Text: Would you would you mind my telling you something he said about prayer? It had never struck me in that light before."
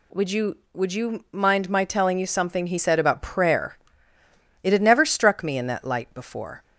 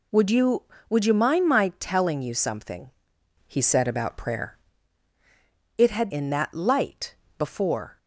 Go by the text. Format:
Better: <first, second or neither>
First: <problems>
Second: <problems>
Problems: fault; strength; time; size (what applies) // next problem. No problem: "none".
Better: first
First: none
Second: pauses between "something" and "he"; noticeable; at 2.8 s; 0.56 s long // skips "never struck me"; at 6.1 s // pauses between "light" and "before"; slight; at 7.1 s; 0.24 s long